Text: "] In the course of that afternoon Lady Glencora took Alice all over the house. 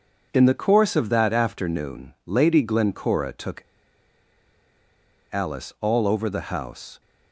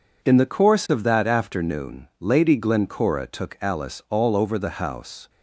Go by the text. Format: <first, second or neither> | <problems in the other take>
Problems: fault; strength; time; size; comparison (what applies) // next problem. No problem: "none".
second | pauses between "took" and "Alice"; strong; at 3.6 s; 1.6 s long